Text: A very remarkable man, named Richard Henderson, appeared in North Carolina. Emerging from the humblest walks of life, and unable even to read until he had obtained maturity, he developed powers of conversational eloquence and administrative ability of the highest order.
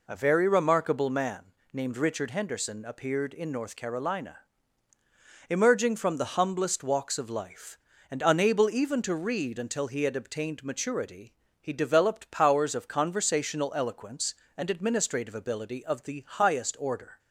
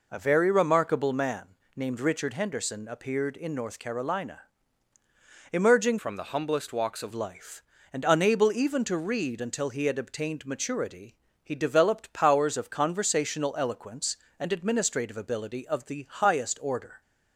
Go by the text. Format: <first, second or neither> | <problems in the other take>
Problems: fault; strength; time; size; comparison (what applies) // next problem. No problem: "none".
first | changes voice from "from" to "of"; from 5.9 to 7.1 s; 1.2 s long